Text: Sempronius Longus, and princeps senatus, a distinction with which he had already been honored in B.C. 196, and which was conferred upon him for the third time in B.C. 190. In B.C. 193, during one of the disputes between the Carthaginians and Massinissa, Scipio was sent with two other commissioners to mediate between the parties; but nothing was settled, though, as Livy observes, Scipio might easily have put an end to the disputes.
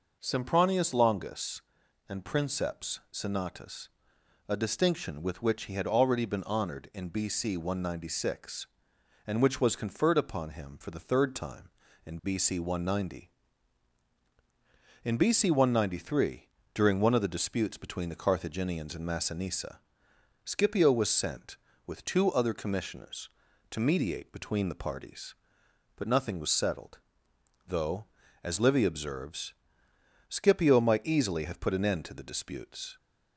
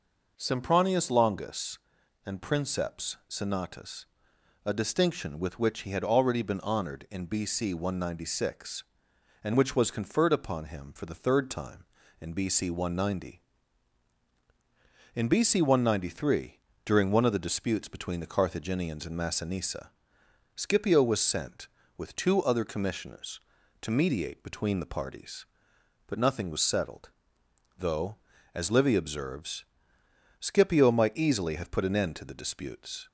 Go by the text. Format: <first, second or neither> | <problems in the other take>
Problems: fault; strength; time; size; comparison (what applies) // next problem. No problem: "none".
neither | none